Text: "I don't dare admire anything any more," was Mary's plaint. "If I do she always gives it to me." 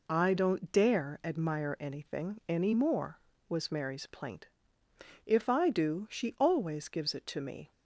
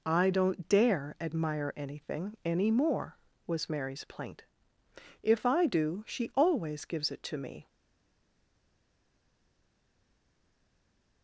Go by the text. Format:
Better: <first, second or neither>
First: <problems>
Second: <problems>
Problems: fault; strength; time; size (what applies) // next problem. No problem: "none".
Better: first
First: none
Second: stays silent after the last word; strong; from 7.6 s on; 3.6 s long